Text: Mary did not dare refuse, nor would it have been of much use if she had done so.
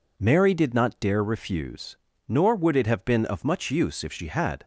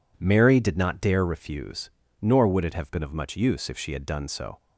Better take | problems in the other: second | stops before "done so"; at 4.6 s

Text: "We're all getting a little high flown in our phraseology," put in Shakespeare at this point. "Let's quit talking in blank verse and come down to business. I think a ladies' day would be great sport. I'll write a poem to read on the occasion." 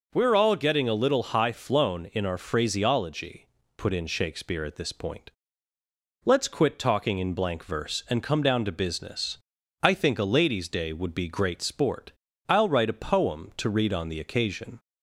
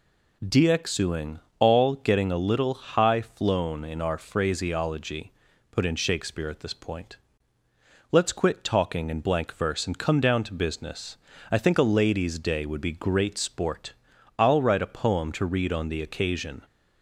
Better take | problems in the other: first | says "Dxuing" for "We're"; at 0.4 s

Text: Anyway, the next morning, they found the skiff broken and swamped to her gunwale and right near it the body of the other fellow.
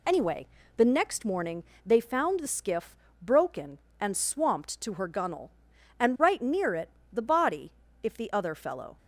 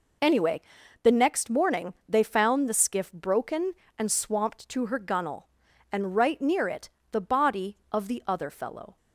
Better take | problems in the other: second | pauses between "skiff" and "broken"; slight; at 2.9 s; 0.26 s long // pauses between "it" and "the"; slight; at 6.8 s; 0.24 s long; slight in the second // says "if" for "of"; at 8.0 s

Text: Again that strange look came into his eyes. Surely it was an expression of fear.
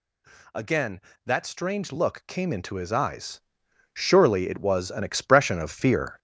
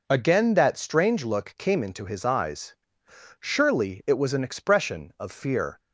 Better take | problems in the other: second | gets louder; noticeable; throughout; 5.5 dB

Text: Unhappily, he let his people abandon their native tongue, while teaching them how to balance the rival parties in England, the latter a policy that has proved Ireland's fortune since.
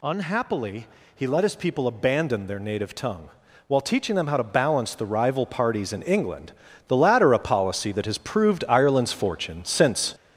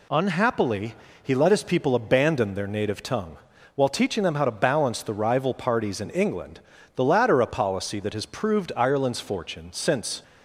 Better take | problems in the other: second | gets louder; noticeable; throughout; 6 dB

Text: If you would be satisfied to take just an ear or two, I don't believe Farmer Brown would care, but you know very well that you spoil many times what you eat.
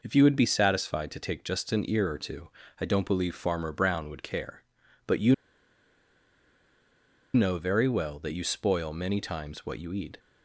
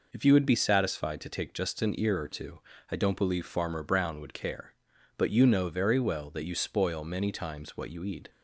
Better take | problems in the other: second | pauses between "you" and "know"; strong; at 5.3 s; 2.0 s long

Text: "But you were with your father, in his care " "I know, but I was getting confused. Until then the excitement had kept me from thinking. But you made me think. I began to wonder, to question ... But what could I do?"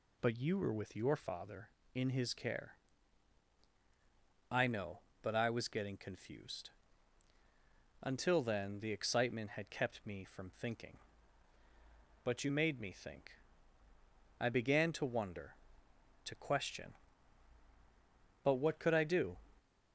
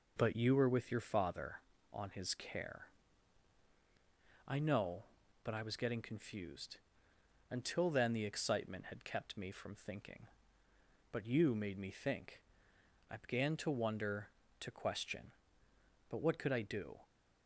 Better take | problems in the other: first | says "on" for "in"; at 1.9 s

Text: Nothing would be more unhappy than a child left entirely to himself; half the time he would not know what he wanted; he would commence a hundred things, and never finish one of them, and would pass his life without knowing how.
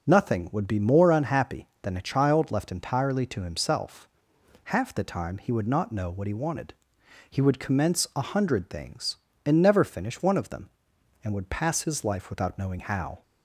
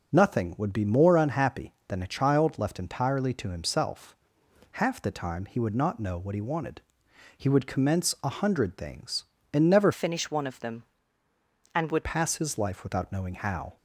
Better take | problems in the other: first | changes voice from "finish" to "would"; from 9.9 to 12.0 s; 2.1 s long

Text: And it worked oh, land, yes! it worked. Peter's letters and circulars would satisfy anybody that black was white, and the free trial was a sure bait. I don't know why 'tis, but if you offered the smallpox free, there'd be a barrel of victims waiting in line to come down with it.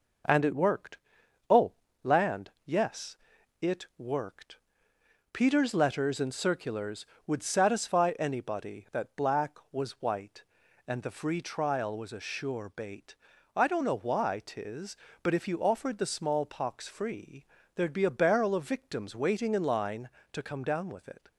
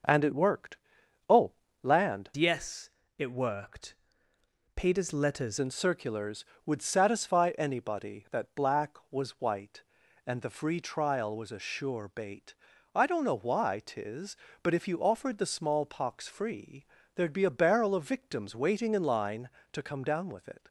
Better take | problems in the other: first | pauses between "worked" and "oh"; noticeable; at 0.7 s; 0.50 s long; noticeable in the first // changes voice from "yes" to "letters"; from 2.3 to 5.5 s; 3.2 s long

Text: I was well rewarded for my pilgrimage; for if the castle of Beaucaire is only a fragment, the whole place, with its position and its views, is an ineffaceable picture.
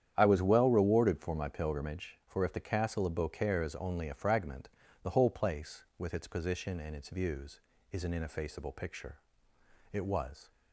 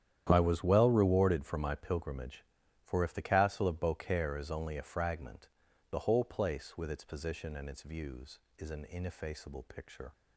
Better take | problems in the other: second | starts louder than the rest; strong; until 1.1 s; 9.5 dB; strong in the second // goes on to say "It was"; from 9.9 s on; 0.58 s long

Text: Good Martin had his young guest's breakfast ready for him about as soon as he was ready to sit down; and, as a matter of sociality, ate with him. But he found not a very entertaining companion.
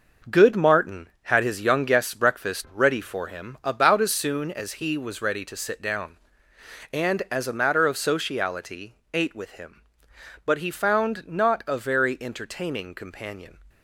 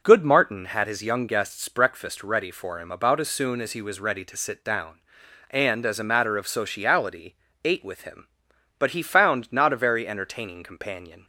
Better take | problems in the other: second | gets quieter; strong; throughout; 7 dB

